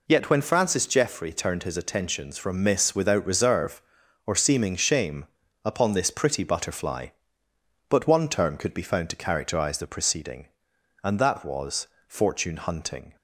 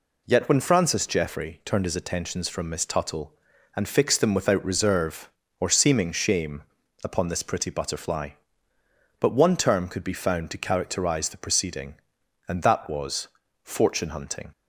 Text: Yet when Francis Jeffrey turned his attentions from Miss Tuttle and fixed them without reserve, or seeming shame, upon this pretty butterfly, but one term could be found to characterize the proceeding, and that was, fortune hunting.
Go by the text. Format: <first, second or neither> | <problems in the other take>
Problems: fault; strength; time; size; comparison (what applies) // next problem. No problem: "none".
second | skips "Tuttle and fixed them"; at 2.9 s